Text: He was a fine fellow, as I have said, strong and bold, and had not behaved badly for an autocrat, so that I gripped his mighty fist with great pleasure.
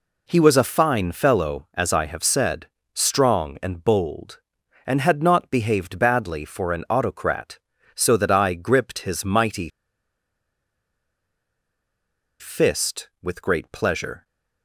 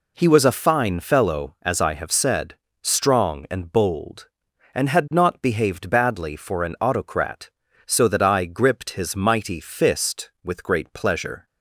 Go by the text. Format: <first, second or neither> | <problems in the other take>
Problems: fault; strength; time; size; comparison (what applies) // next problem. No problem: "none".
second | pauses between "mighty" and "fist"; strong; at 9.6 s; 2.7 s long